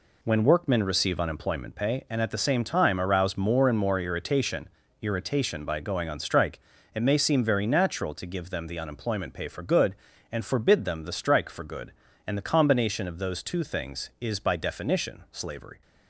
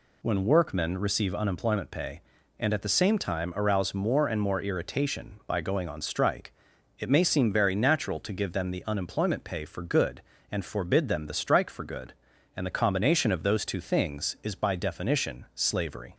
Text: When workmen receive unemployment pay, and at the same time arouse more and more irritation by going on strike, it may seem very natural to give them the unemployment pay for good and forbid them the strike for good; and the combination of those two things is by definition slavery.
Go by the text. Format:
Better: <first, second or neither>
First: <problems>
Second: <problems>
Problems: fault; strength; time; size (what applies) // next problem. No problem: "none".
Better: second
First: says "irritation" twice; at 5.0 s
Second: none